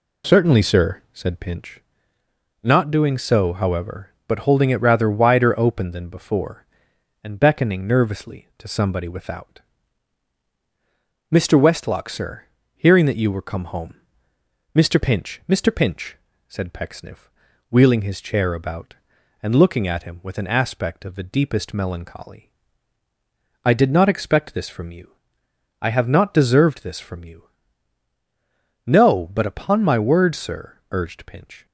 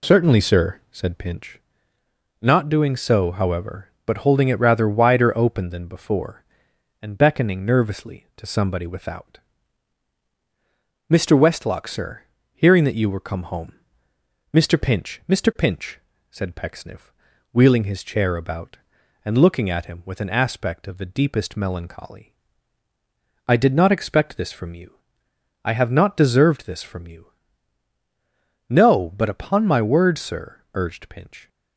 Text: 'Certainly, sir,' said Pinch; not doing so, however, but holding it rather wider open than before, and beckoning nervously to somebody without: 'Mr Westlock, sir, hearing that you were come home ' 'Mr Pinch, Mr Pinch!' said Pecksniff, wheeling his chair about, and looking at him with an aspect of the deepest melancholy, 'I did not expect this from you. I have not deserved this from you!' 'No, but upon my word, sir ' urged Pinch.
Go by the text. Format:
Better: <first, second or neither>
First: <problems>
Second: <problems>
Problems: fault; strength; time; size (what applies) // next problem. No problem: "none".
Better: neither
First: none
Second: none